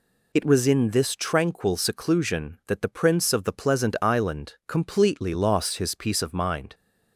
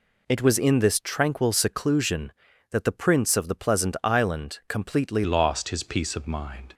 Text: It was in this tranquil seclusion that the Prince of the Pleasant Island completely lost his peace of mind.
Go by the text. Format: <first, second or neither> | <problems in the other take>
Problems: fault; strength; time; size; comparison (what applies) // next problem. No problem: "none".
first | changes voice at "lost"; from 5.2 s on; 1.5 s long